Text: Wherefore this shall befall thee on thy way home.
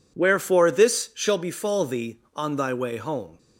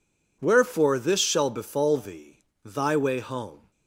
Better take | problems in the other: first | skips "on"; at 2.5 s

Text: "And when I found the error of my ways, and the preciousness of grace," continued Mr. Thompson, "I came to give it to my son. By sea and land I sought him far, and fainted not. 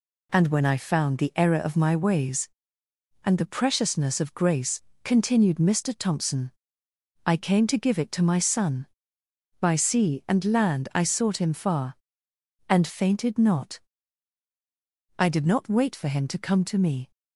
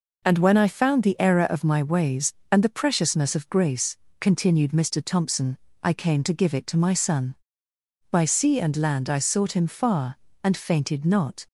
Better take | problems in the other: second | goes on to say "I did not wait for him to come to me"; strong; from 15.1 s on; 1.9 s long

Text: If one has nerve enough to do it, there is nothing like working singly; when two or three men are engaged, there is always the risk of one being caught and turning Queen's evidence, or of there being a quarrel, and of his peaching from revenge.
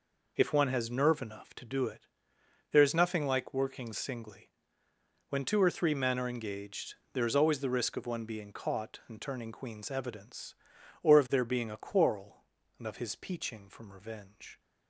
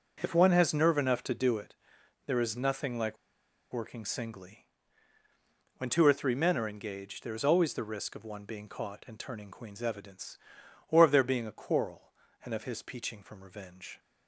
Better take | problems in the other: first | starts louder than the rest; until 1.2 s; 6.5 dB // pauses between "like" and "working"; noticeable; at 3.1 s; 0.56 s long

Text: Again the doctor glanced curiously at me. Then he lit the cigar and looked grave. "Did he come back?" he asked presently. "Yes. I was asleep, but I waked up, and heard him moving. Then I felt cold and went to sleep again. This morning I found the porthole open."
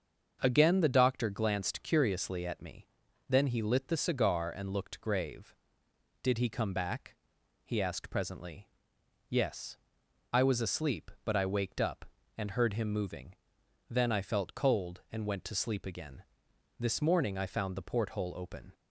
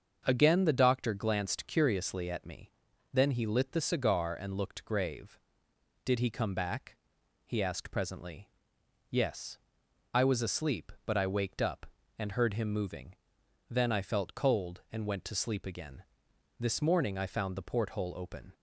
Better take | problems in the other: neither | starts louder than the rest; the same in both

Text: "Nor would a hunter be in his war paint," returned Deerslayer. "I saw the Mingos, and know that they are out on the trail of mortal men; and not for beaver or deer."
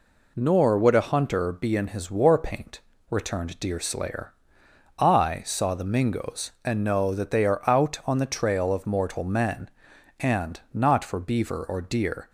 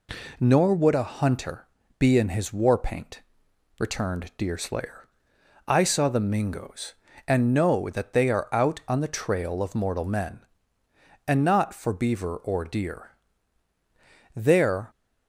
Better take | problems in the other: first | pauses between "hunter" and "be"; slight; at 1.6 s; 0.32 s long // goes on to say "There"; from 14.3 s on; 0.56 s long

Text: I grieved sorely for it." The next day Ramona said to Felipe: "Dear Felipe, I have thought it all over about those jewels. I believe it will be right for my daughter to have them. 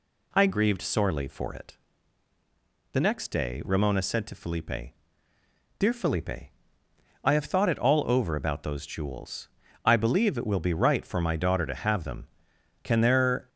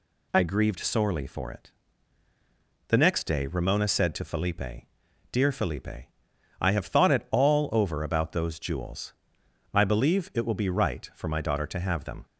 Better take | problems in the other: second | goes on to say "Can there"; noticeable; from 12.8 s on; 0.66 s long

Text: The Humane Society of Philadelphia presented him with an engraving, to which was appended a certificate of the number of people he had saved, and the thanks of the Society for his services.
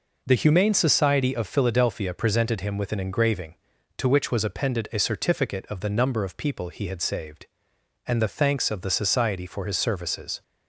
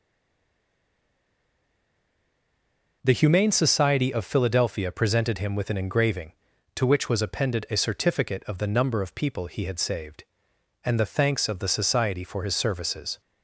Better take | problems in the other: first | stays silent before the first word; strong; until 3.0 s; 3.0 s long

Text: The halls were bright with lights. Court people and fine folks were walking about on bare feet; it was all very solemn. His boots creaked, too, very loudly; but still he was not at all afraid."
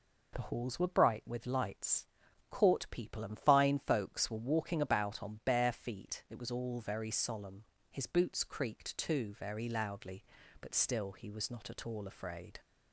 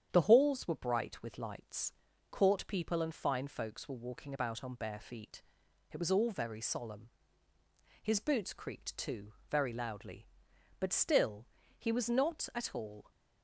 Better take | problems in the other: first | starts louder than the rest; strong; until 1.1 s; 9 dB // pauses between "still" and "he"; slight; at 11.4 s; 0.34 s long // stops before "afraid"; at 13.1 s

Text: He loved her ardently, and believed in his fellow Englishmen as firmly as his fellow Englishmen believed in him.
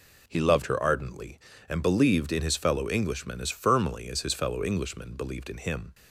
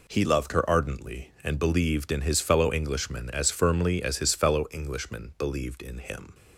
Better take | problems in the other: neither | none

